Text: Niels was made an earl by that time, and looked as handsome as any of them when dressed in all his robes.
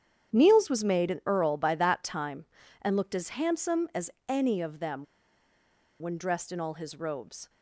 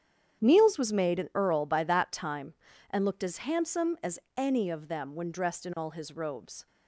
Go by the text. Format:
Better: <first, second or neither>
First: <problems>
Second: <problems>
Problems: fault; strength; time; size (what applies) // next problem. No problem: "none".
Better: second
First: starts louder than the rest; strong; until 1.3 s; 9 dB // pauses between "as" and "any"; slight; at 4.1 s; 0.18 s long // pauses between "them" and "when"; noticeable; at 5.0 s; 0.95 s long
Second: starts louder than the rest; strong; until 1.4 s; 9 dB // pauses between "as" and "any"; slight; at 4.1 s; 0.18 s long